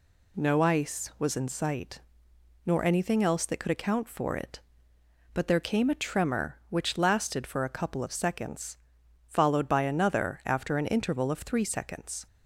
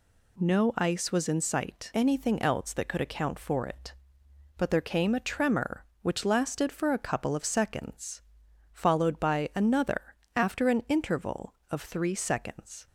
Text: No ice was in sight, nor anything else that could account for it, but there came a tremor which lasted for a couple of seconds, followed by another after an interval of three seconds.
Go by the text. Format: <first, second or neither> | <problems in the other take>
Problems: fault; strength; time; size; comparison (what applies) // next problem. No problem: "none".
first | skips "nor"; at 1.9 s // pauses between "another" and "after"; slight; at 10.1 s; 0.22 s long